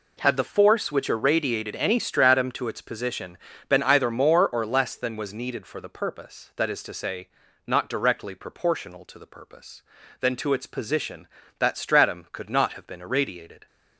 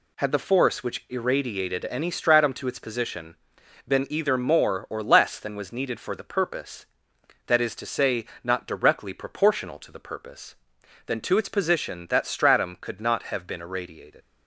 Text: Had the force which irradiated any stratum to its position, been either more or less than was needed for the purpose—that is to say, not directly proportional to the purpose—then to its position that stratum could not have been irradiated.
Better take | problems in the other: first | leaves "irradiated" unfinished; at 14.2 s; 115 ms

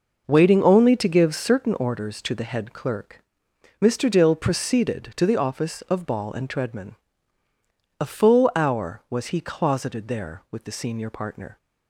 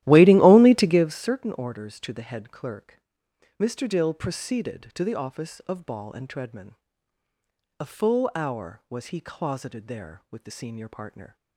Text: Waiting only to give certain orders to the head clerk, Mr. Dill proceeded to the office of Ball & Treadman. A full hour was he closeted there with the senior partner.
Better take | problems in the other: first | starts louder than the rest; strong; until 1.2 s; 14.5 dB

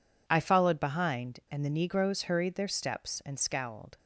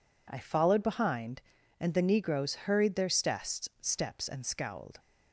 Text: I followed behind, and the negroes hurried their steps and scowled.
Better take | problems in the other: first | says "steps" twice; at 3.8 s

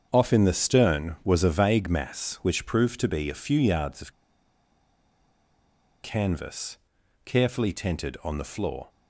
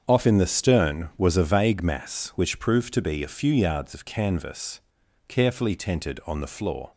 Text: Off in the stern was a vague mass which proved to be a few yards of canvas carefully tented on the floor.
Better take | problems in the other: second | starts louder than the rest; strong; until 1.1 s; 7.5 dB; strong in the second // pauses between "of" and "canvas"; strong; at 4.1 s; 1.9 s long // pauses between "canvas" and "carefully"; noticeable; at 6.7 s; 0.48 s long; noticeable in the second

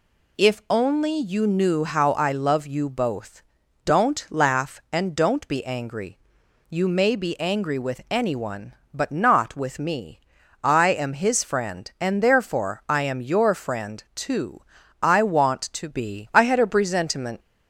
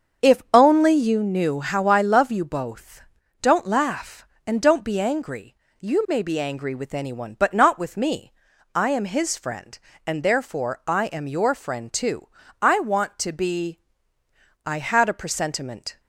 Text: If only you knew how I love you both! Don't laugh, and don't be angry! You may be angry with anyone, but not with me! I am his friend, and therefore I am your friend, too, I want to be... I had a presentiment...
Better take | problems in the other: first | starts louder than the rest; until 1.2 s; 7 dB

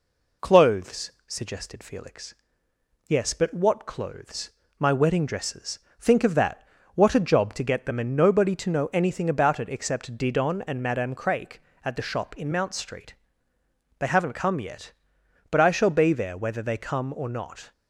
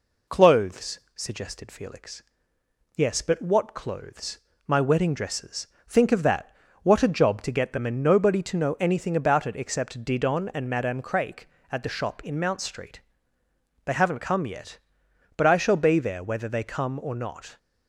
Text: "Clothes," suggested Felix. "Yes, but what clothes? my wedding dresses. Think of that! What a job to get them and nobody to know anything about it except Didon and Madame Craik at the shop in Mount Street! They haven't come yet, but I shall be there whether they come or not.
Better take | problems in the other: neither | none

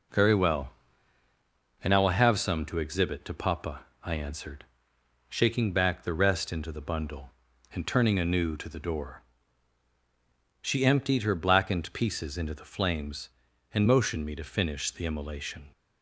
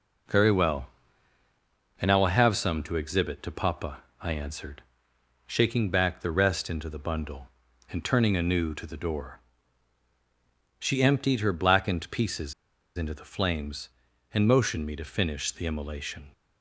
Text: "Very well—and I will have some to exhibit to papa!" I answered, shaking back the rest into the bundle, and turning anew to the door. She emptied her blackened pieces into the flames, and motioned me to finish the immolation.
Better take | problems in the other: first | pauses between "pieces" and "into"; at 12.5 s; 0.44 s long

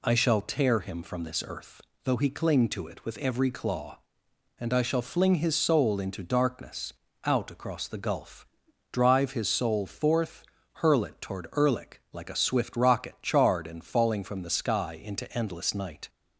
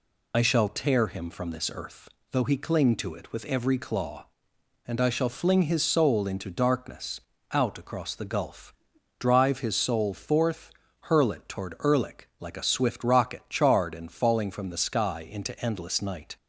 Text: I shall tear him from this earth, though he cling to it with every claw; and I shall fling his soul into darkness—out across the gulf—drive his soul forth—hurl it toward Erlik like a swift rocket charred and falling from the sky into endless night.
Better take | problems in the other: first | loses the start of "I"; at 0.3 s; 45 ms

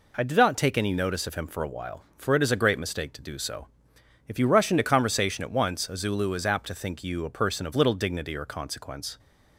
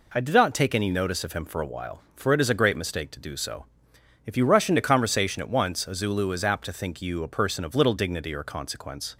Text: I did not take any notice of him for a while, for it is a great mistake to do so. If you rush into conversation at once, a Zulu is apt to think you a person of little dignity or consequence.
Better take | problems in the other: neither | none

